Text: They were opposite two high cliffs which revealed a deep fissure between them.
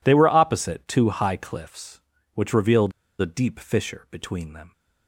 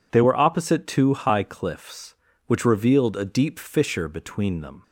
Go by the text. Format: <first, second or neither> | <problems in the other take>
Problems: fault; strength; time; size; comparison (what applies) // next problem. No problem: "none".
second | pauses between "revealed" and "a"; slight; at 2.9 s; 0.30 s long